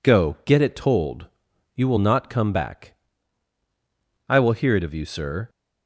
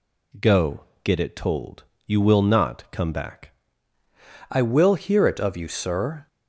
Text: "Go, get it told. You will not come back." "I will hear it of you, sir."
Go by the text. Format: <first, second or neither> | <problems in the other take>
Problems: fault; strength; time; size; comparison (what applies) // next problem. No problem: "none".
first | changes voice at "I"; from 4.4 s on; 1.8 s long